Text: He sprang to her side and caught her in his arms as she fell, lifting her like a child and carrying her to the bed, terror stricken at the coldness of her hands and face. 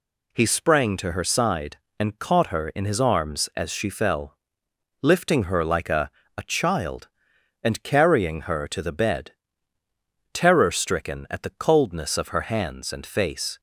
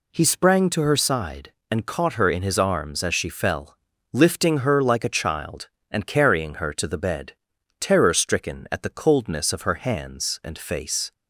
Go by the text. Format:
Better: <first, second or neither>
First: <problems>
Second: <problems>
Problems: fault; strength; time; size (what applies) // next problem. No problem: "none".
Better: second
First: says "a" twice; at 6.3 s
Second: none